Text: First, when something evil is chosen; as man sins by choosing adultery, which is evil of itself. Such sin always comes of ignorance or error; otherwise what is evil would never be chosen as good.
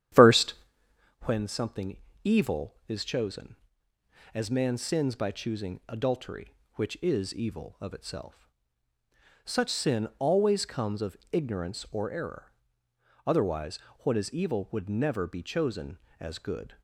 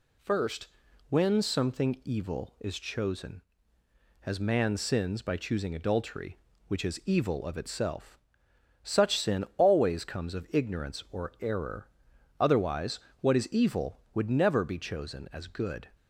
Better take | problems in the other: second | starts louder than the rest; strong; until 1.3 s; 10.5 dB // pauses between "something" and "evil"; slight; at 1.9 s; 0.26 s long // pauses between "of" and "ignorance"; slight; at 11.1 s; 0.16 s long // pauses between "otherwise" and "what"; slight; at 13.7 s; 0.28 s long; slight in the second

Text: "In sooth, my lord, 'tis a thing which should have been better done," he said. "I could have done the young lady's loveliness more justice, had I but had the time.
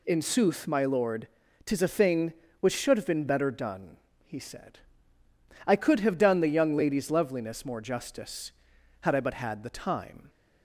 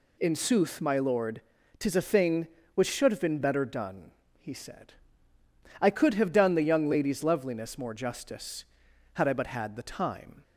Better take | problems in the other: neither | none

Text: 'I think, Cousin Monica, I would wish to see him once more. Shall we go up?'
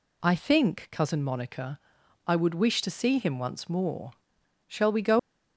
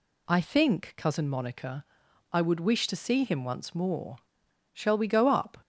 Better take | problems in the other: second | stops before "up"; at 5.1 s

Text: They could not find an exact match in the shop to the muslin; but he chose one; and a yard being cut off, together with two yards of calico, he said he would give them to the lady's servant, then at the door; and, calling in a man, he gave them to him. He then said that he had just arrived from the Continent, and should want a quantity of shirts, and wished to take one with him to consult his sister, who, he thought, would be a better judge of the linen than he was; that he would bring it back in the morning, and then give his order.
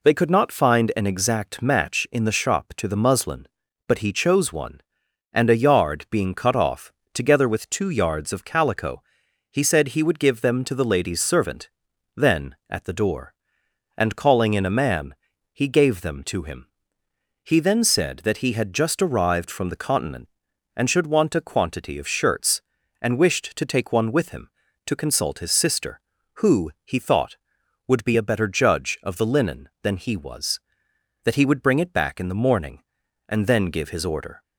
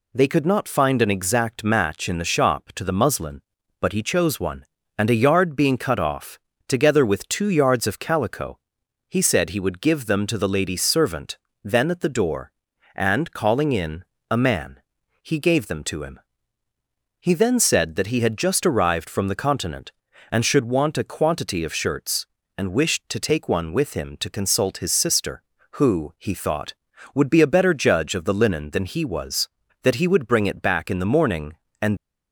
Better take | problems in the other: first | pauses between "in" and "a"; slight; at 14.0 s; 0.28 s long // stops before "then give his order"; at 31.9 s

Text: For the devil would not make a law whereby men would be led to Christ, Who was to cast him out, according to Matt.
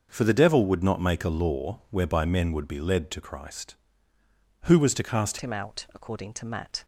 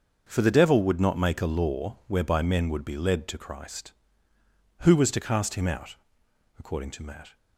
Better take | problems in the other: second | starts louder than the rest; until 1.1 s; 6.5 dB; also in the second // changes voice at "him"; from 5.4 s on; 1.4 s long

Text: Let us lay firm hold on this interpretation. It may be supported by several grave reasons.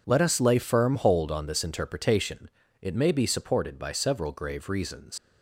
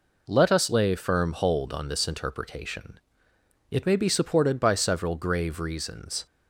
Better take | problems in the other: second | leaves "reasons" unfinished; at 5.1 s; 95 ms

